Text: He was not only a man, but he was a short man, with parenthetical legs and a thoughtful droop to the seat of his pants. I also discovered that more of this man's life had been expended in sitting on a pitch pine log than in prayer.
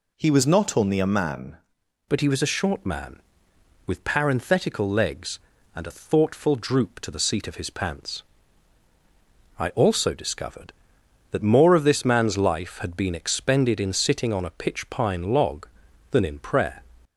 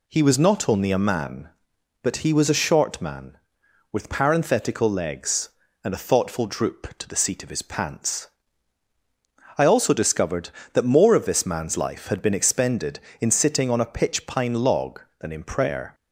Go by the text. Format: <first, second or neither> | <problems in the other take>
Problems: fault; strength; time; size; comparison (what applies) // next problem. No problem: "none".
second | changes voice at "but"; from 2.0 s on; 14.8 s long